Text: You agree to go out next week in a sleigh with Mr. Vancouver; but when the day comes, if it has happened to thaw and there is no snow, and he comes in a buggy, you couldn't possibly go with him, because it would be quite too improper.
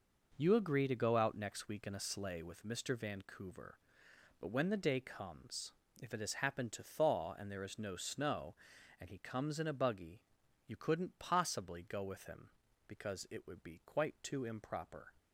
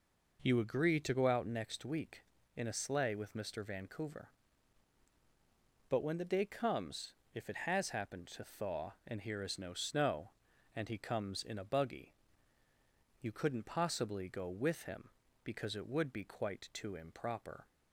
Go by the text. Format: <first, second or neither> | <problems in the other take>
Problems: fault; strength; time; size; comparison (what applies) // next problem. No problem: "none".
first | says "here" for "there"; at 9.2 s